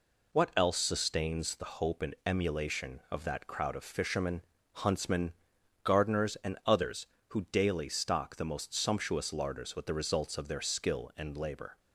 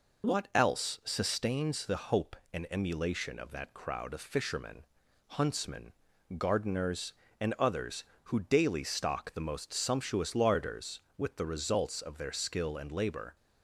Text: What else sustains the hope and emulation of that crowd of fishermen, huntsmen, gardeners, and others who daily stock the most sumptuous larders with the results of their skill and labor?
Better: neither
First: none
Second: none

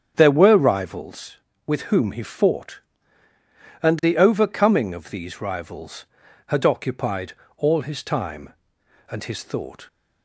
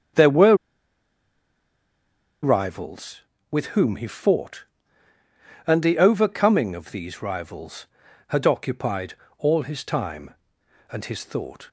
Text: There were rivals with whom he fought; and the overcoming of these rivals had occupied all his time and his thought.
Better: first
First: starts louder than the rest; strong; until 1.1 s; 8 dB // pauses between "occupied" and "all"; slight; at 7.3 s; 0.24 s long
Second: starts louder than the rest; strong; until 3.0 s; 8 dB // pauses between "were" and "rivals"; strong; at 0.5 s; 1.8 s long // pauses between "occupied" and "all"; slight; at 9.1 s; 0.24 s long

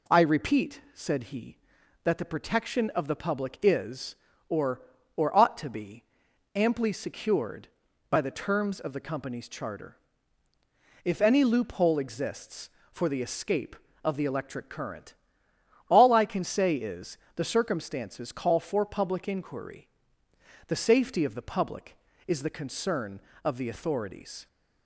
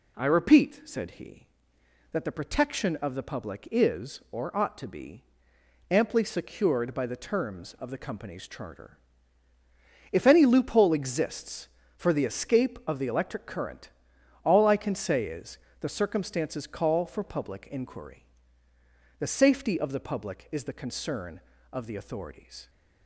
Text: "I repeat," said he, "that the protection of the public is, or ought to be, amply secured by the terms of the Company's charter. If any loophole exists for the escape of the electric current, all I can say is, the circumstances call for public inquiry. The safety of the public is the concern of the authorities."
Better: second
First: says "or" twice; at 5.1 s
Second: none

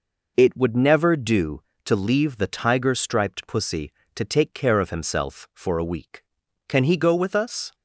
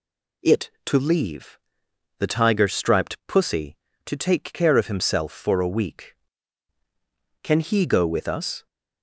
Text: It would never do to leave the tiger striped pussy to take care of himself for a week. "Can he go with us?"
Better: first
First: none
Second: skips "would never do"; at 0.7 s // pauses between "leave" and "the"; noticeable; at 1.5 s; 0.60 s long

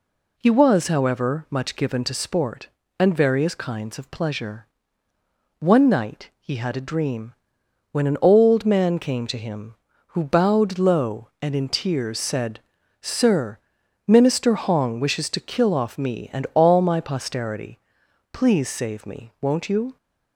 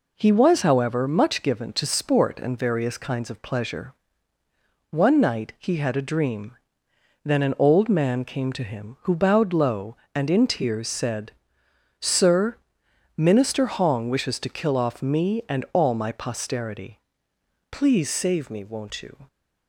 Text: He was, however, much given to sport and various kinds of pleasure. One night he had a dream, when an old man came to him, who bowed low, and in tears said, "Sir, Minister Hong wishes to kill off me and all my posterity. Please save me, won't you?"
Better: first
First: none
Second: says "then" for "when"; at 7.2 s

